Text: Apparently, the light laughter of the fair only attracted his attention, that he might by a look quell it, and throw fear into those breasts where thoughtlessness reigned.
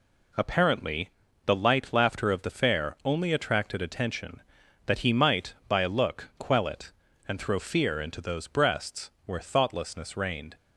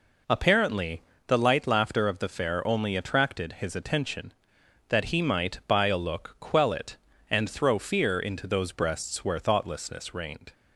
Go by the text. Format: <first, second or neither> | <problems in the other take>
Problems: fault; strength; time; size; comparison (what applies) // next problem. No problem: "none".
second | skips "his"; at 3.8 s